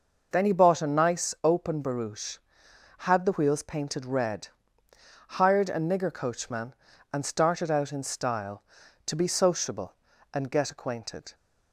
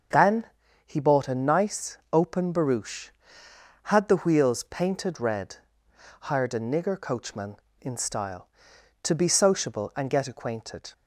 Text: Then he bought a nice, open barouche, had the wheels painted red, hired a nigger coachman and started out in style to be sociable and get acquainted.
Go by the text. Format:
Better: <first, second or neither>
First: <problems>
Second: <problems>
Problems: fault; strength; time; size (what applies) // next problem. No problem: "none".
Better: first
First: none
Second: starts louder than the rest; until 1.5 s; 6.5 dB // pauses between "Then" and "he"; at 0.4 s; 0.40 s long // skips "and started out"; at 7.6 s